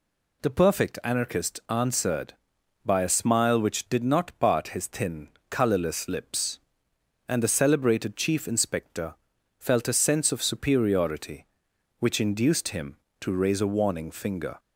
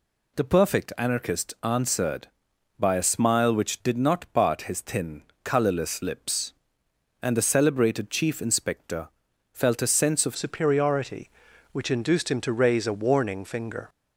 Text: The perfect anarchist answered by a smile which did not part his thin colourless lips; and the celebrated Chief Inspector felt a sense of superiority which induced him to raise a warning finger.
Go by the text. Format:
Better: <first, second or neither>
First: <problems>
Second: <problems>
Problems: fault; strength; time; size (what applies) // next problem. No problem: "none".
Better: first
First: pauses between "thin" and "colourless"; slight; at 5.2 s; 0.18 s long // pauses between "Inspector" and "felt"; at 9.1 s; 0.44 s long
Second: pauses between "thin" and "colourless"; slight; at 5.2 s; 0.18 s long // pauses between "Inspector" and "felt"; at 9.0 s; 0.44 s long // changes voice at "superiority"; from 10.3 s on; 3.5 s long